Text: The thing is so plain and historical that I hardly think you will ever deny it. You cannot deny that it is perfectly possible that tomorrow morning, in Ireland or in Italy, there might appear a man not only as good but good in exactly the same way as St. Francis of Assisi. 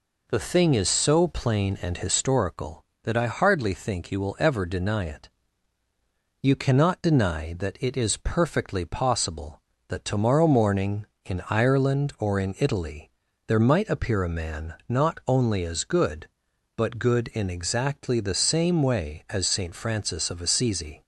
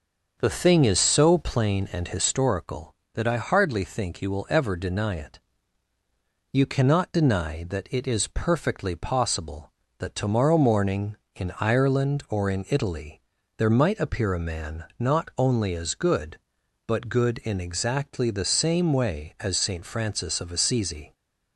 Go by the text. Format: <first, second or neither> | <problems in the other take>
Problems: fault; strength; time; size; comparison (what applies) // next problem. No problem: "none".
first | starts louder than the rest; until 1.8 s; 6.5 dB // pauses between "man" and "not"; slight; at 14.8 s; 0.16 s long; slight in the first